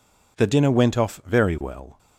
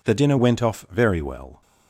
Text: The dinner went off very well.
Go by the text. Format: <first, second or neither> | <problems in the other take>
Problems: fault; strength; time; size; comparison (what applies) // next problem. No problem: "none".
neither | none